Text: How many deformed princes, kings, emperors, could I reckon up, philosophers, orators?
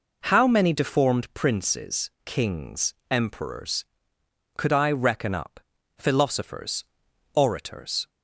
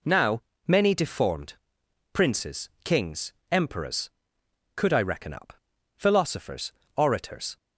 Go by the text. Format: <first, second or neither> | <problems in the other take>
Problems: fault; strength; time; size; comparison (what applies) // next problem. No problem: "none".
first | says "Now" for "How"; at 0.0 s // pauses between "deformed" and "princes"; noticeable; at 1.5 s; 0.58 s long